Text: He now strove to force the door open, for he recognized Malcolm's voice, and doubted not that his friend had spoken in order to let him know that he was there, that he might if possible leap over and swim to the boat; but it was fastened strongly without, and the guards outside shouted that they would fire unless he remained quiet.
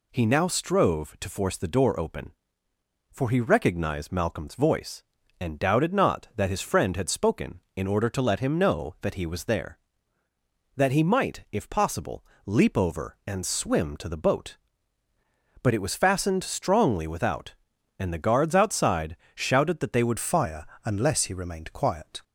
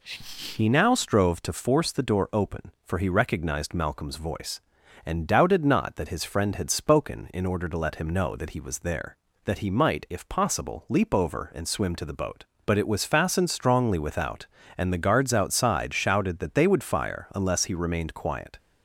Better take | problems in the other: second | pauses between "possible" and "leap"; slight; at 12.2 s; 0.22 s long // pauses between "outside" and "shouted"; slight; at 19.1 s; 0.20 s long // changes voice at "fire"; from 20.1 s on; 2.1 s long // pauses between "fire" and "unless"; slight; at 20.6 s; 0.20 s long

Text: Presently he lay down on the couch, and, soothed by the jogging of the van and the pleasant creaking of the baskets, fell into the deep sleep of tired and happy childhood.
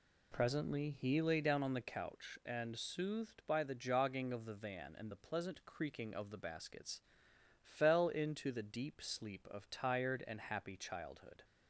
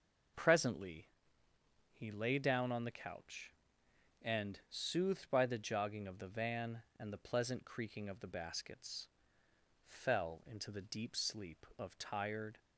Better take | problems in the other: first | pauses between "Presently" and "he"; noticeable; at 1.0 s; 0.86 s long // stops before "and happy childhood"; at 12.5 s

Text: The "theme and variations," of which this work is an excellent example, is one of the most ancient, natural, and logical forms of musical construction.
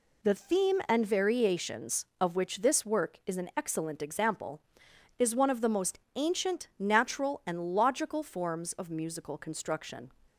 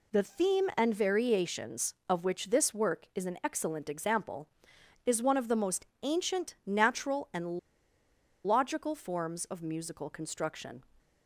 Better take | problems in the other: first | pauses between "most" and "ancient"; slight; at 5.8 s; 0.20 s long; slight in the first // pauses between "and" and "logical"; noticeable; at 7.5 s; 0.85 s long

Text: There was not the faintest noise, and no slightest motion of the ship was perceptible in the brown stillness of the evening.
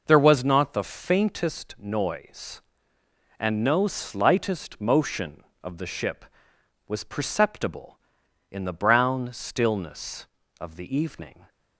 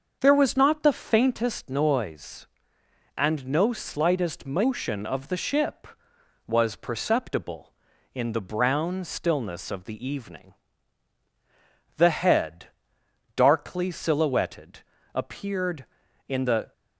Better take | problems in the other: first | starts louder than the rest; until 1.2 s; 6.5 dB // goes on to say "The head darkly silhouetted appeared in the"; strong; from 11.9 s on; 4.7 s long

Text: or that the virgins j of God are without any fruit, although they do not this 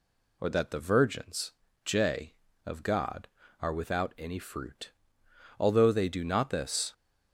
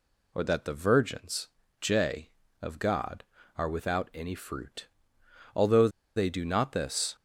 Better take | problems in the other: first | pauses between "virgins" and "j"; slight; at 1.4 s; 0.32 s long; slight in the first // pauses between "although" and "they"; slight; at 5.8 s; 0.27 s long

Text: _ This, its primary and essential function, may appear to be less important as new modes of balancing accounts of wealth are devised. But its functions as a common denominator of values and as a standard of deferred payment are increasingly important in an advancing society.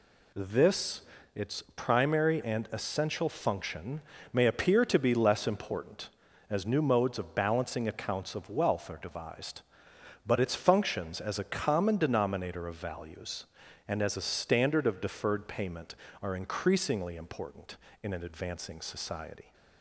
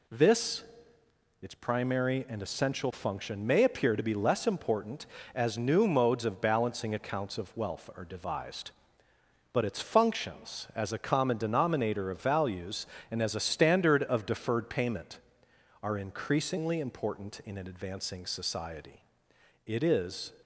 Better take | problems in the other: first | goes on to say "It is"; noticeable; from 19.6 s on; 0.66 s long

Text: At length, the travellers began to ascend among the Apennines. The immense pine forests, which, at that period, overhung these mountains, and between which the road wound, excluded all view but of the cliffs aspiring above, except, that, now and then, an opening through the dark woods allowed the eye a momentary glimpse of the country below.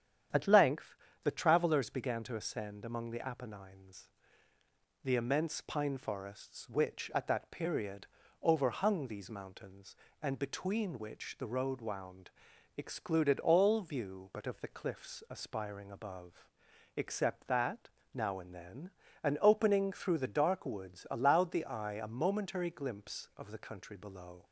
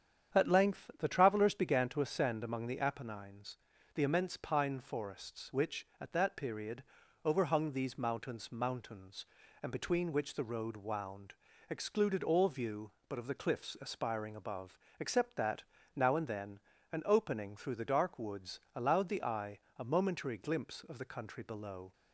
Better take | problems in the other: first | starts louder than the rest; strong; until 1.4 s; 8.5 dB; strong in the first // says "mountains" twice; at 8.5 s // pauses between "woods" and "allowed"; slight; at 18.5 s; 0.16 s long // pauses between "eye" and "a"; slight; at 19.5 s; 0.20 s long

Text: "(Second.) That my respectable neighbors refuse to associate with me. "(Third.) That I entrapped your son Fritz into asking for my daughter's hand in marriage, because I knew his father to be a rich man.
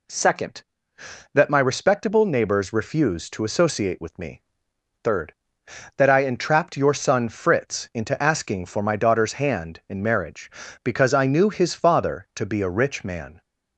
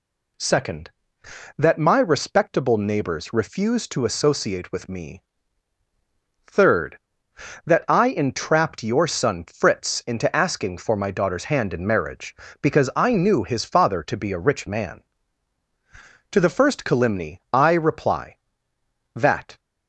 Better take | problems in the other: first | goes on to say "To the first calumny I reply that"; strong; from 16.3 s on; 3.2 s long

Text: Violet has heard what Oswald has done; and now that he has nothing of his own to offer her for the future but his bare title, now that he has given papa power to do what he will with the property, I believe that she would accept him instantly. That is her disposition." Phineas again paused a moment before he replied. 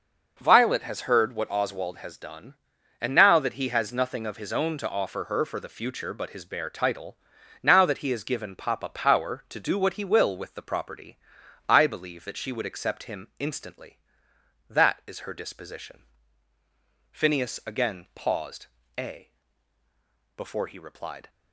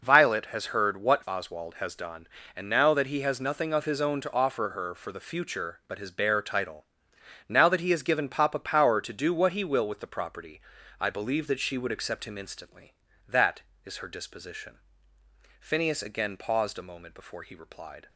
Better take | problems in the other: second | pauses between "paused" and "a"; slight; at 18.6 s; 0.32 s long // skips "moment"; at 19.8 s

